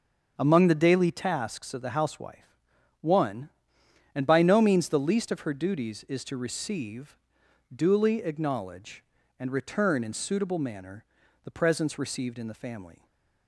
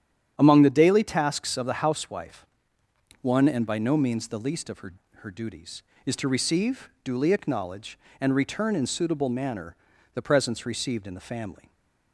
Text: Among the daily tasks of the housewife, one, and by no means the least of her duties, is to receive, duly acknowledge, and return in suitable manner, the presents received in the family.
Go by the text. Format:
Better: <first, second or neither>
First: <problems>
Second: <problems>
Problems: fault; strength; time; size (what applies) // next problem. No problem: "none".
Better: first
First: starts louder than the rest; until 1.4 s; 7 dB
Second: starts louder than the rest; strong; until 1.3 s; 9.5 dB // says "her" twice; at 5.1 s